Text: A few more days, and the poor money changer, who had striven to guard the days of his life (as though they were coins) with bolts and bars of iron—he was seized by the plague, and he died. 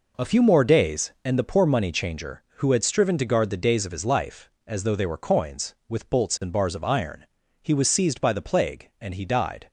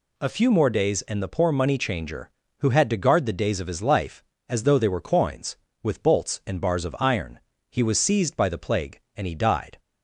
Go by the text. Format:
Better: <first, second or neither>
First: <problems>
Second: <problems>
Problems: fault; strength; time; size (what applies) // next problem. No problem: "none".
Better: first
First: none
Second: skips "striven"; at 2.8 s